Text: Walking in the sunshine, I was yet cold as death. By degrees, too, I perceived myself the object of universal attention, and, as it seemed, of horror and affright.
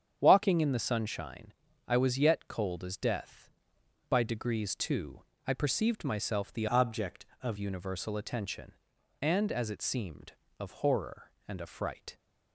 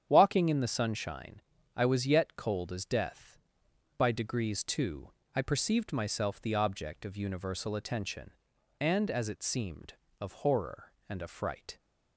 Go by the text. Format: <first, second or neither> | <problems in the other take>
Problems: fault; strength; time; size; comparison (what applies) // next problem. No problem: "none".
second | starts louder than the rest; strong; until 1.2 s; 8.5 dB; strong in the second // changes voice from "object" to "of"; from 6.6 to 7.5 s; 0.9 s long